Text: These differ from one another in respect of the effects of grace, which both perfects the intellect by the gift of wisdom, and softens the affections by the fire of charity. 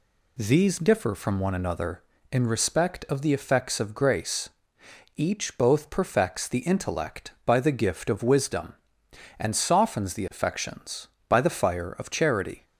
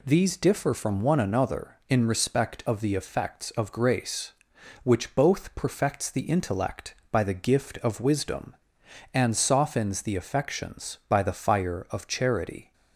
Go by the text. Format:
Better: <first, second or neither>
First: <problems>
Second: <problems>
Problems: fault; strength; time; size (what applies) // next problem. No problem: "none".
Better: second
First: says "each" for "which"; at 5.1 s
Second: none